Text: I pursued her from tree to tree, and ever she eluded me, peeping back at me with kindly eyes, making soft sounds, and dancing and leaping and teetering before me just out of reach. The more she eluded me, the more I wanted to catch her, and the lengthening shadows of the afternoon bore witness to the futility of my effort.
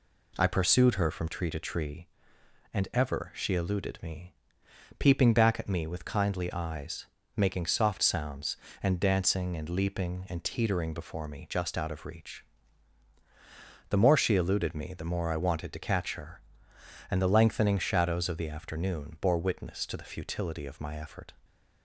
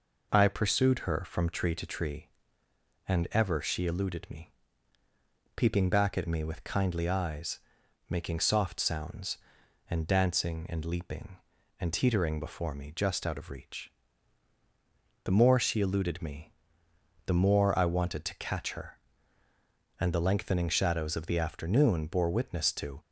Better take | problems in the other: first | stops before "the futility of my effort"; at 22.9 s

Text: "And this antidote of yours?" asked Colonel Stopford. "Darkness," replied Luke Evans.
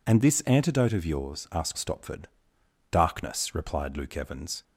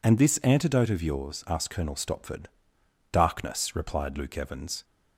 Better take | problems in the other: second | skips "Colonel"; at 1.7 s

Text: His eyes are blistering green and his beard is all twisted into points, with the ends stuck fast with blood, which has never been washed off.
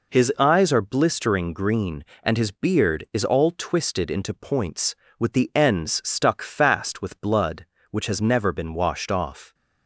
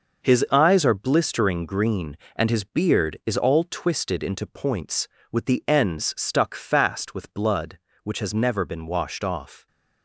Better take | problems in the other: first | gets quieter; strong; throughout; 8.5 dB

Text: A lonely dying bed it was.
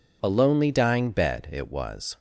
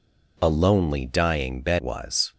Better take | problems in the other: first | skips "it"; at 1.8 s

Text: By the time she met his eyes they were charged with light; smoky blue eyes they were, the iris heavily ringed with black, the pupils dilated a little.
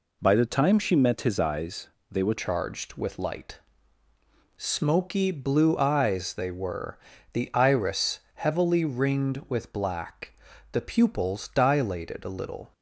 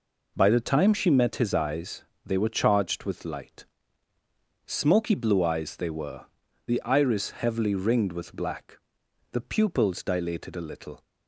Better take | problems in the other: second | pauses between "eyes" and "they"; slight; at 1.8 s; 0.24 s long; slight in the second // changes voice at "charged"; from 2.3 s on; 10.4 s long // pauses between "iris" and "heavily"; slight; at 8.1 s; 0.16 s long

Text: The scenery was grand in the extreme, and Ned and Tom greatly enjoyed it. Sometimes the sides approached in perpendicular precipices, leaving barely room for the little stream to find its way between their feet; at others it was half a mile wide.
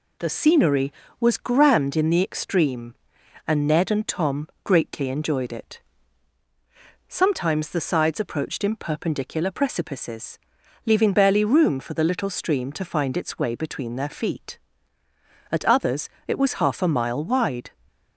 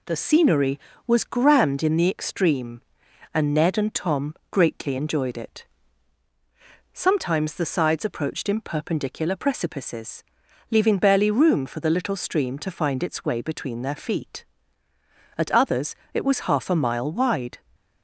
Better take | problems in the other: neither | pauses between "Tom" and "greatly"; slight; the same in both // pauses between "others" and "it"; slight; the same in both

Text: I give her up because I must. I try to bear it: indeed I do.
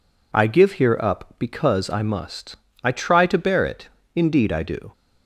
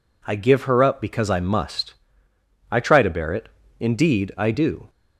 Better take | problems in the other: second | says "here" for "her"; at 0.7 s

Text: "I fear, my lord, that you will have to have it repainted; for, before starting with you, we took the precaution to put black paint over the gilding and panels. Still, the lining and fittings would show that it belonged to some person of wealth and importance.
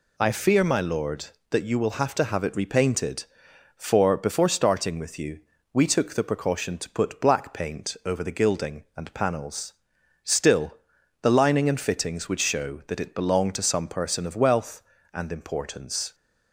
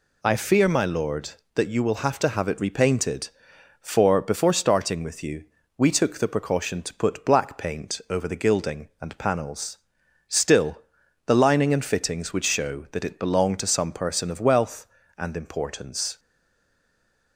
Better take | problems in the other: first | stays silent after the last word; noticeable; from 16.1 s on; 1.2 s long

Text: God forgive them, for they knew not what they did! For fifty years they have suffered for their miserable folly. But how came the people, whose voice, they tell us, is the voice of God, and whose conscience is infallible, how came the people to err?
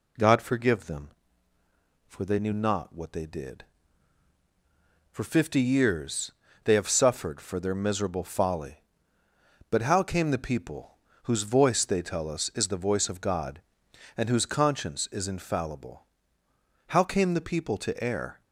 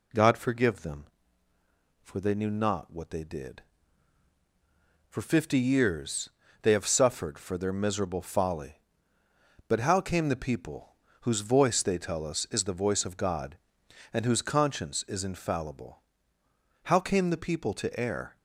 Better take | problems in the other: neither | pauses between "years" and "they"; slight; the same in both

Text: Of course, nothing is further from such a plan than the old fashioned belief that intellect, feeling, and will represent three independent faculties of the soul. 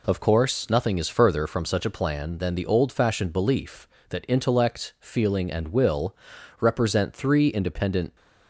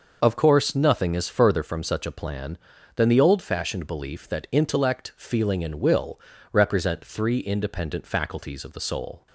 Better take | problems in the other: second | pauses between "will" and "represent"; noticeable; at 6.1 s; 0.46 s long; slight in the second // stops before "faculties of the soul"; at 8.1 s

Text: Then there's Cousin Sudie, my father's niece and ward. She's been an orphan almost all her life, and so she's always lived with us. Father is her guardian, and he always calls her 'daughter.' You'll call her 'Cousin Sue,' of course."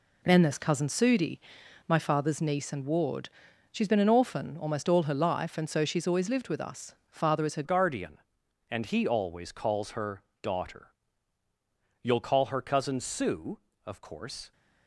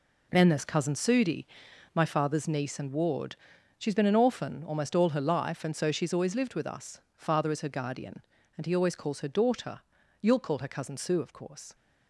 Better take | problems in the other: second | changes voice at "guardian"; from 7.6 s on; 6.9 s long // pauses between "her" and "daughter"; slight; at 10.2 s; 0.20 s long

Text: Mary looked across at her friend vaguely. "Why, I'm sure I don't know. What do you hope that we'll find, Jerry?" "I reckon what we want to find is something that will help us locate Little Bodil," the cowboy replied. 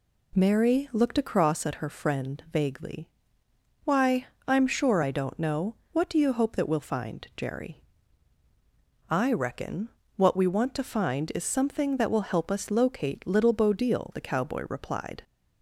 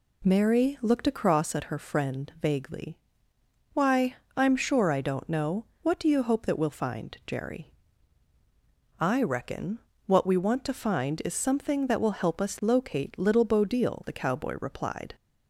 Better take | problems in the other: neither | pauses between "reckon" and "what"; slight; the same in both

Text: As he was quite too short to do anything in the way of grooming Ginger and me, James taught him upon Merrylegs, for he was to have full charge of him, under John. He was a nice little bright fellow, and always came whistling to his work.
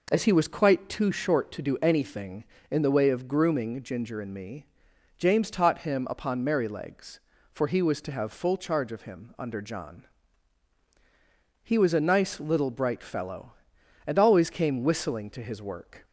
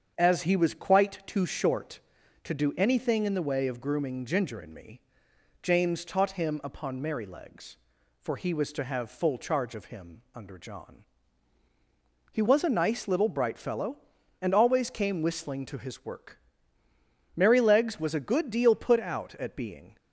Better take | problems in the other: first | starts louder than the rest; strong; until 1.1 s; 7.5 dB // goes on to say "Merrylegs was a good deal put out at being"; strong; from 17.3 s on; 2.6 s long

